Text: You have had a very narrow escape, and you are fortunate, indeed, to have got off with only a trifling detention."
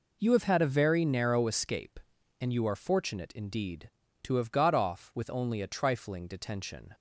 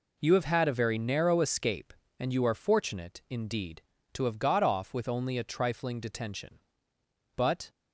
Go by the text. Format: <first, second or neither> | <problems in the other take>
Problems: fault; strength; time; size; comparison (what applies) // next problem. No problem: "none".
first | goes on to say "But"; slight; from 7.3 s on; 0.34 s long